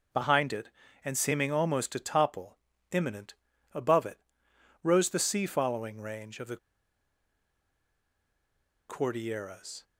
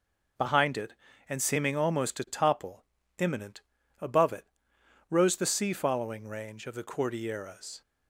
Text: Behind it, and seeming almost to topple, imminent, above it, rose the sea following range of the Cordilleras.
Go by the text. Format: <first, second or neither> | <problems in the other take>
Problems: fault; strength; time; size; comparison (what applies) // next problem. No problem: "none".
second | pauses between "the" and "Cordilleras"; strong; at 6.5 s; 2.3 s long